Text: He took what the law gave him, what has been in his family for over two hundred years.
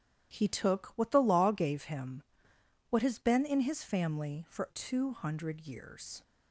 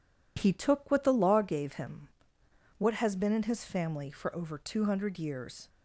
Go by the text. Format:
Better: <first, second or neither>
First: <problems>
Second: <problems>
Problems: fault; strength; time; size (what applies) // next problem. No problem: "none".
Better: second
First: starts louder than the rest; strong; until 1.3 s; 11 dB // skips "over"; at 4.6 s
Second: none